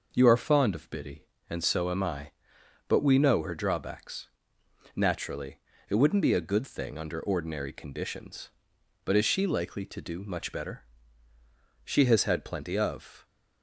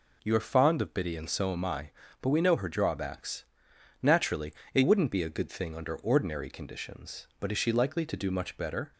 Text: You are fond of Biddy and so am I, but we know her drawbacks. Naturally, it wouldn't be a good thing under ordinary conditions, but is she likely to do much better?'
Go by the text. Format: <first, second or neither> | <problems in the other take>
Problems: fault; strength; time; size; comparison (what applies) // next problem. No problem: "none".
second | goes on to say "She has had plenty of"; from 11.8 s on; 1.4 s long